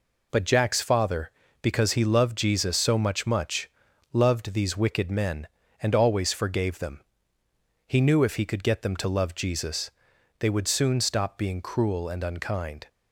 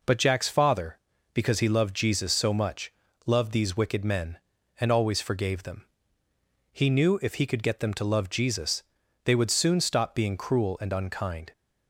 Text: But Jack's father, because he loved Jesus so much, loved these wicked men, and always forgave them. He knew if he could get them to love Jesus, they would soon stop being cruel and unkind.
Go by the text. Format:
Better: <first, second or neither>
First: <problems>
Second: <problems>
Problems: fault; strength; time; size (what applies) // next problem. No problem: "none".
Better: second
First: says "much" twice; at 3.2 s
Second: none